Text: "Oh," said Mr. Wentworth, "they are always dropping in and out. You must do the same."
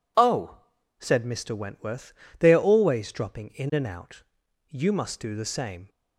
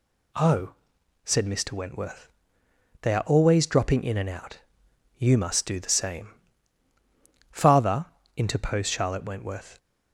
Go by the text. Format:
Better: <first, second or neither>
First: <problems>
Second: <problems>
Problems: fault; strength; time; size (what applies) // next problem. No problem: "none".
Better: first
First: none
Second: goes on to say "Father interposed Charlotte Wentworth"; strong; from 7.5 s on; 2.2 s long